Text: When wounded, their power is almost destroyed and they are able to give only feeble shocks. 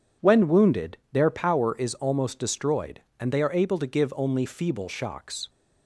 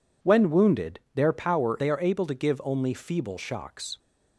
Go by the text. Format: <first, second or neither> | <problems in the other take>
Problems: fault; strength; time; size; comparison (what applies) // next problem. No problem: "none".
first | skips "is almost destroyed and"; at 1.7 s